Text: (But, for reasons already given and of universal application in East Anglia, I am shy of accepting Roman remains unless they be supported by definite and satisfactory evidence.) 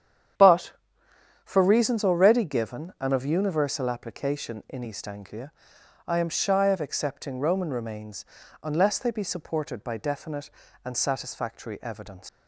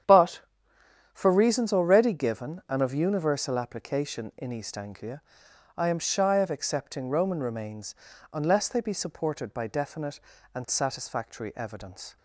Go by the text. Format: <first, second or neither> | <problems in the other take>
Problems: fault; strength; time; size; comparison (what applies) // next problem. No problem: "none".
second | starts louder than the rest; strong; until 2.1 s; 9 dB; strong in the second // pauses between "remains" and "unless"; at 8.2 s; 0.38 s long; also in the second // leaves "evidence" unfinished; at 12.2 s; 140 ms